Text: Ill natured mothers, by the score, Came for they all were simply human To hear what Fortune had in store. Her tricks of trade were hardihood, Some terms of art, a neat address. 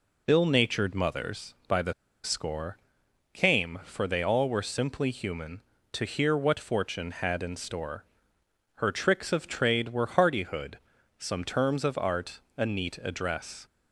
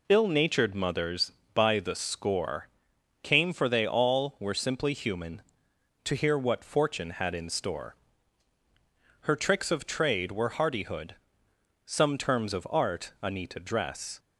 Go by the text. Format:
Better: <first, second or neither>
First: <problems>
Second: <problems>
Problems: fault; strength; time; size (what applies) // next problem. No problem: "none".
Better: second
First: pauses between "the" and "score"; slight; at 1.9 s; 0.30 s long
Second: none